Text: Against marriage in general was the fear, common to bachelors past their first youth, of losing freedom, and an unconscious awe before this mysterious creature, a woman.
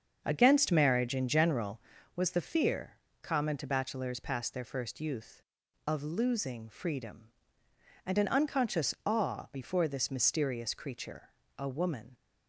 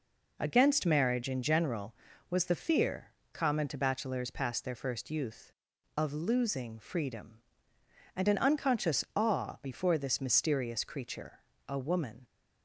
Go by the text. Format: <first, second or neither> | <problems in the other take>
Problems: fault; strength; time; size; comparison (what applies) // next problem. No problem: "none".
second | starts louder than the rest; until 2.1 s; 7 dB